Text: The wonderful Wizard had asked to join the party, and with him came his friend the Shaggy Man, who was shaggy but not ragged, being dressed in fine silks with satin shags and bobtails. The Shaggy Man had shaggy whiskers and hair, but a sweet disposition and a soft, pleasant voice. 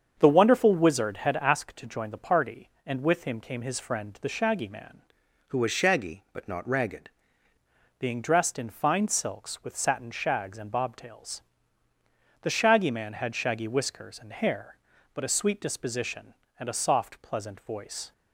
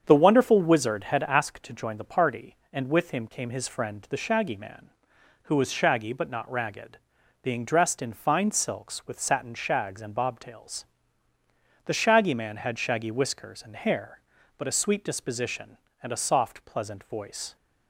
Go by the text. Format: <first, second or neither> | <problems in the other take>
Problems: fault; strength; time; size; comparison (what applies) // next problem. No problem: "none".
second | starts louder than the rest; strong; until 1.1 s; 7.5 dB; strong in the second // changes voice from "who" to "ragged"; from 5.5 to 7.0 s; 1.5 s long